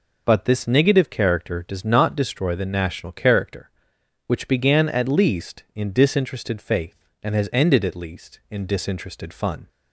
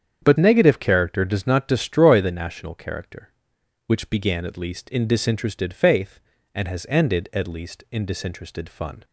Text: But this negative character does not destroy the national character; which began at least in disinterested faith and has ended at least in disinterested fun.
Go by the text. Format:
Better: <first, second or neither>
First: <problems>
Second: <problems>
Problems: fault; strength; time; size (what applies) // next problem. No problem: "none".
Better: first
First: none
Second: starts louder than the rest; strong; until 1.2 s; 8 dB // skips "this"; at 0.3 s